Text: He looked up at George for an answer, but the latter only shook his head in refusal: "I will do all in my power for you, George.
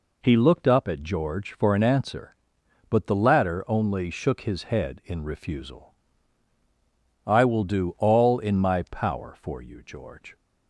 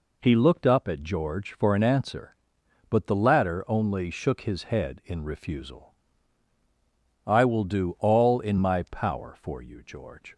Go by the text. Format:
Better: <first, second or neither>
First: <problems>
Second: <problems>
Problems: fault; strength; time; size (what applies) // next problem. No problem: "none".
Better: neither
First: none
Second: none